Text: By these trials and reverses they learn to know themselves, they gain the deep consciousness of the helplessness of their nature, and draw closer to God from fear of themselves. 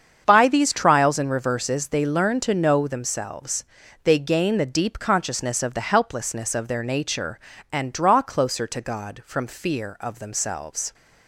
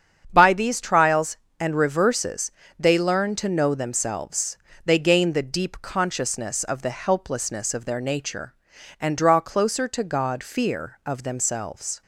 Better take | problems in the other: first | starts louder than the rest; strong; until 1.3 s; 7.5 dB; strong in the first // pauses between "reverses" and "they"; slight; at 2.5 s; 0.26 s long // skips "from"; at 10.4 s

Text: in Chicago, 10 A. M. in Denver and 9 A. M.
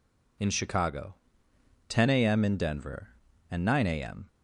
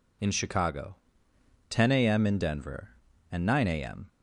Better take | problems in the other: neither | none

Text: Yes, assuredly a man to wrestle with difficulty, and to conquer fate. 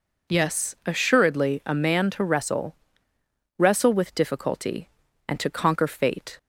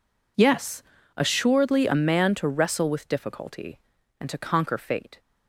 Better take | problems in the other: second | says "wrestle" twice; at 3.5 s

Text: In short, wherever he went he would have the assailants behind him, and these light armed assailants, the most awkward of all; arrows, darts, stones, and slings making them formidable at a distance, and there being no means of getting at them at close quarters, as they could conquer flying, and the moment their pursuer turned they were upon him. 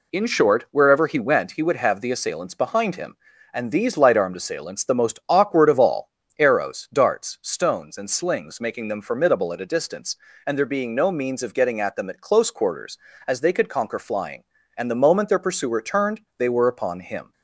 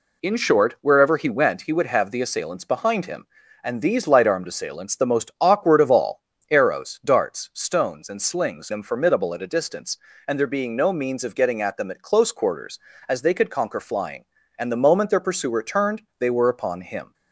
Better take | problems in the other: first | skips "making"; at 8.7 s // pauses between "turned" and "they"; slight; at 16.0 s; 0.18 s long; slight in the first

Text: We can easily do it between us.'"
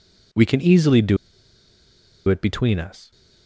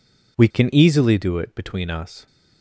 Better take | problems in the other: second | pauses between "do" and "it"; at 1.1 s; 1.1 s long

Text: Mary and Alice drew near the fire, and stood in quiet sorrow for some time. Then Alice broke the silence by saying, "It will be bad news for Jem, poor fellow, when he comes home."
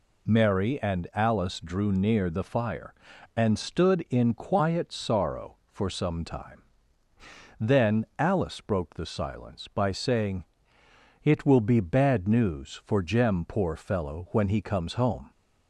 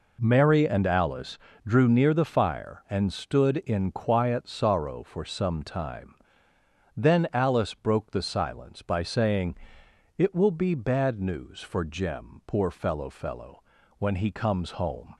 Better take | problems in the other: first | pauses between "Alice" and "drew"; slight; at 1.3 s; 0.28 s long // says "fellow" twice; at 13.0 s

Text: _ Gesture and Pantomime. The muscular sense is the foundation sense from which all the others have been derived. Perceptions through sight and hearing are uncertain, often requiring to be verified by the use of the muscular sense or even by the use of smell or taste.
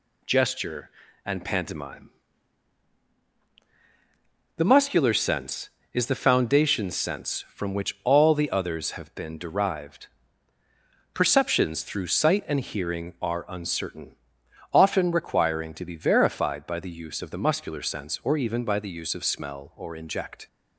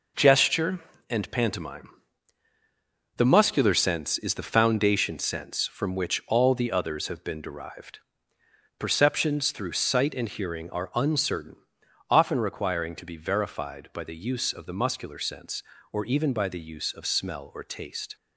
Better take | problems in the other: second | says "inject" for "taste"; at 19.9 s

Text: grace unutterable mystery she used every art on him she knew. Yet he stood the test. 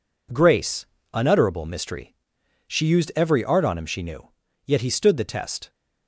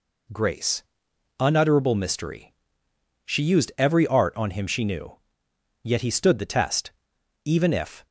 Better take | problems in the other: first | pauses between "grace" and "unutterable"; noticeable; at 0.8 s; 0.58 s long; slight in the first // pauses between "mystery" and "she"; noticeable; at 2.5 s; 0.72 s long; noticeable in the first // goes on to say "Even if"; noticeable; from 7.4 s on; 0.62 s long

